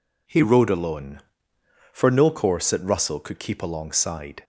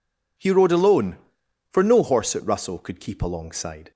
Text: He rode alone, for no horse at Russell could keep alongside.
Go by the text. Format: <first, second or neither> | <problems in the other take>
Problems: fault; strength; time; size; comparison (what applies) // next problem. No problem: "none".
second | says "course" for "horse"; at 2.3 s